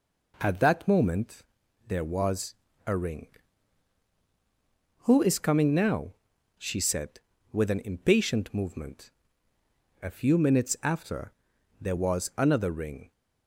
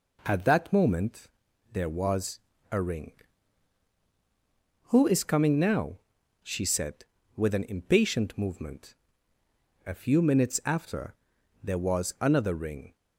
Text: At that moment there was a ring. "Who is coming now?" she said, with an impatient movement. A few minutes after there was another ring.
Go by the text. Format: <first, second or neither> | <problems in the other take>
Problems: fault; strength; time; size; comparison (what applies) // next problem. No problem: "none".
neither | pauses between "moment" and "there"; the same in both // pauses between "was" and "a"; slight; the same in both // pauses between "after" and "there"; noticeable; the same in both